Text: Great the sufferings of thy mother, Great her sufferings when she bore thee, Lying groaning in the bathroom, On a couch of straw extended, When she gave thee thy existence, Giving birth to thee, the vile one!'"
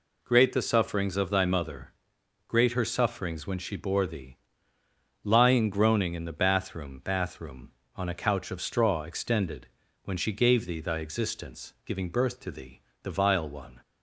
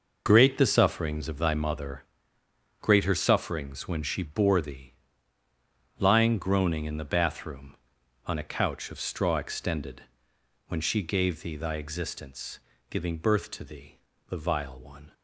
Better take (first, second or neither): second